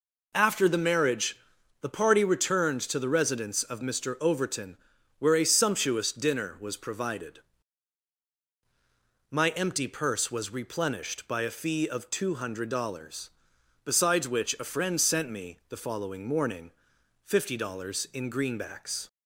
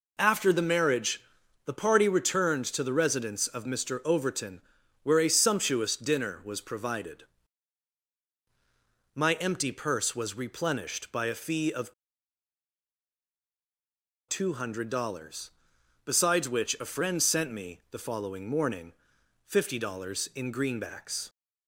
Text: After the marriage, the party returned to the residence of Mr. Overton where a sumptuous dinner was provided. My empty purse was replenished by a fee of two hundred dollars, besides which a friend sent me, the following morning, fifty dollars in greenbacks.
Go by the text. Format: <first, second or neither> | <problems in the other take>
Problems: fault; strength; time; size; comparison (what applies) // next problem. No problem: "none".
first | pauses between "Overton" and "where"; at 4.6 s; 0.42 s long; also in the first // pauses between "of" and "two"; strong; at 11.9 s; 2.3 s long